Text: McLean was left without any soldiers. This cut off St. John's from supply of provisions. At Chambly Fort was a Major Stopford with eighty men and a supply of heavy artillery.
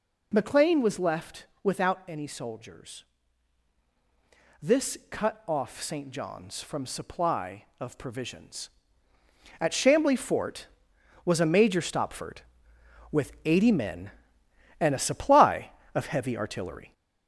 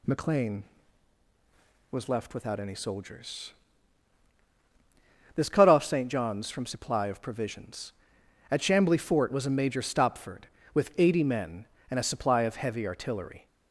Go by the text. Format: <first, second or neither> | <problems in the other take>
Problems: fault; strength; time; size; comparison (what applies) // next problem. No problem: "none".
second | gets louder; throughout; 3.5 dB // pauses between "left" and "without"; slight; at 1.4 s; 0.18 s long